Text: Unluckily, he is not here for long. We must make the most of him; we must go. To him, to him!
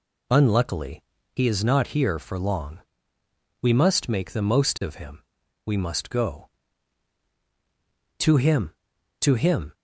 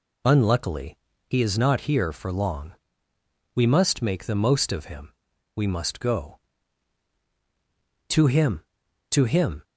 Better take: neither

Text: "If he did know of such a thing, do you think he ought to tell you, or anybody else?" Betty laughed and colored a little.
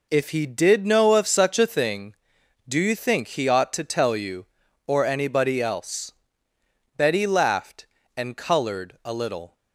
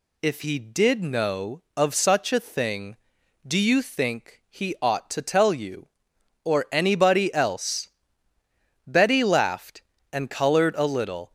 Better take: neither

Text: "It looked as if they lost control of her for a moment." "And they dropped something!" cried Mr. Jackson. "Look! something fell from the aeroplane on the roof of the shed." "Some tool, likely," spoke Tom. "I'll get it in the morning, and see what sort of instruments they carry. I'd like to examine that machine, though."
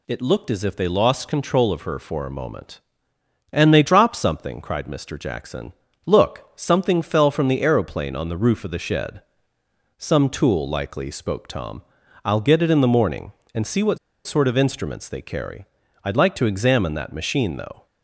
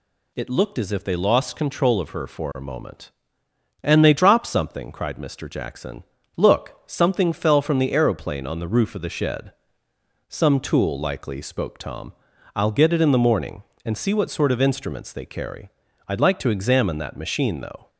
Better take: second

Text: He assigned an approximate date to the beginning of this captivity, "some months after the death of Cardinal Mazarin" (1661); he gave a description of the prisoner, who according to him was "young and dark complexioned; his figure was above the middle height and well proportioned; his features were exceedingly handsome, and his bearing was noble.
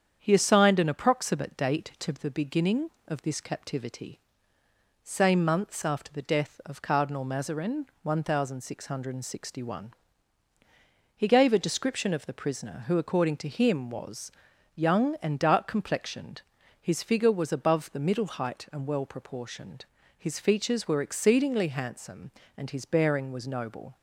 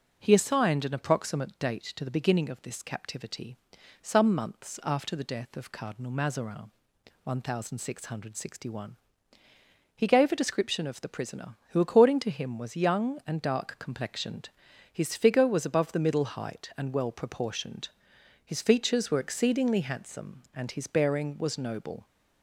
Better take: second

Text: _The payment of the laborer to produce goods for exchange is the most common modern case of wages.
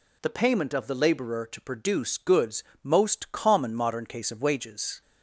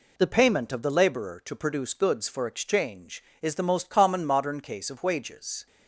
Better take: second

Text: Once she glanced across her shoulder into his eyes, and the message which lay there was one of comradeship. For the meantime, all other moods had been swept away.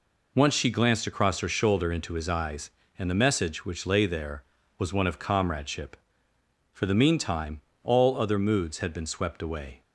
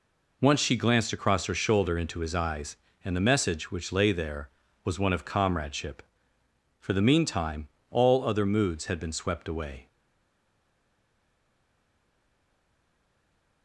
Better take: first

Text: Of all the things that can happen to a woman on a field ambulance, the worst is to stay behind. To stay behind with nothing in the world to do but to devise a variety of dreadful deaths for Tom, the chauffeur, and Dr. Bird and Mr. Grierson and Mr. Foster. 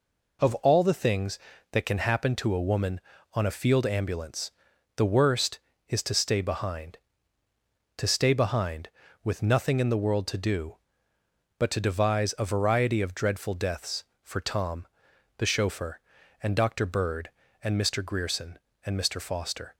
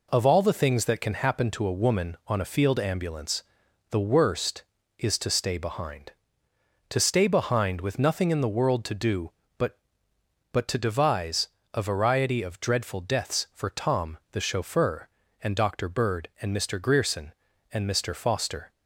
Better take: first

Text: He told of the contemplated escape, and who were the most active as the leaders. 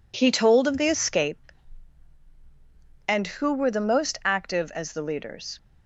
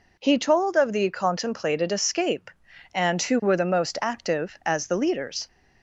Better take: second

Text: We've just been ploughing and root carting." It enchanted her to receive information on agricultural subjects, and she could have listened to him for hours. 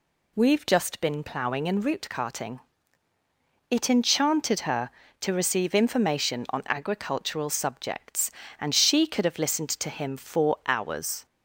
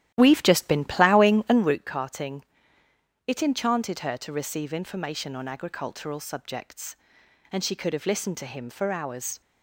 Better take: first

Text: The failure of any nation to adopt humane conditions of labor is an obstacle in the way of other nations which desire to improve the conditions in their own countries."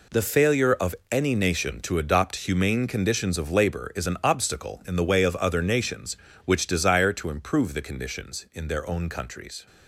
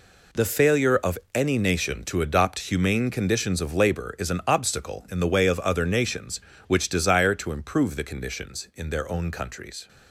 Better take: neither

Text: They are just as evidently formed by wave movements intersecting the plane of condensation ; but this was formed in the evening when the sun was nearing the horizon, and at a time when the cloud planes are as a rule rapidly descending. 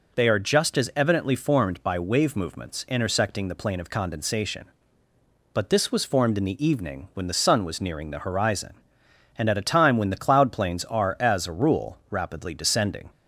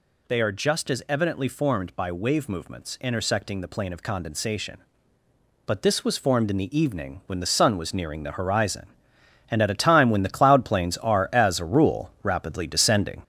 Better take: first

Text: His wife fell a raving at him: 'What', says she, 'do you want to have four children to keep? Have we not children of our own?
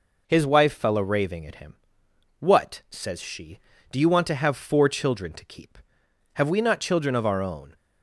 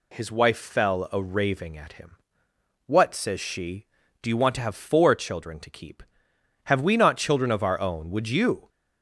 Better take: first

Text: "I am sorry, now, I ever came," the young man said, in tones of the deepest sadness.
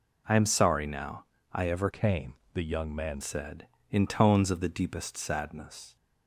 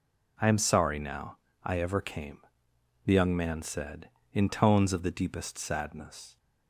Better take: second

